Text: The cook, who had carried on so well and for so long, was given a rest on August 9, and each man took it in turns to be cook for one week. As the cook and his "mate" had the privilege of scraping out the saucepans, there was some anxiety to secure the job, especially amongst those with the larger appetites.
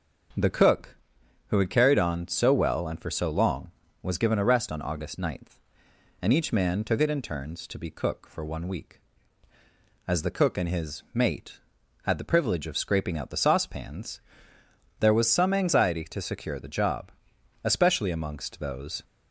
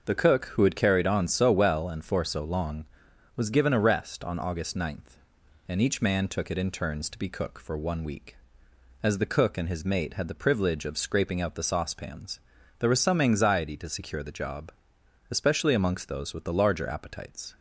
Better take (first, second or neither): second